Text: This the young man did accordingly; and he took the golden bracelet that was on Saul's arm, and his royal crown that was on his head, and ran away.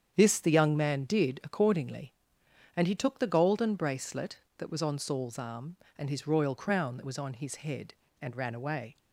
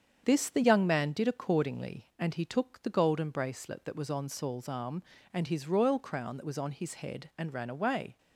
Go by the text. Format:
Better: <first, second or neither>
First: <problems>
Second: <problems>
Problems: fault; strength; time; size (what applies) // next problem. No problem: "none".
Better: neither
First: starts louder than the rest; strong; until 1.1 s; 8 dB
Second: starts louder than the rest; strong; until 1.2 s; 7.5 dB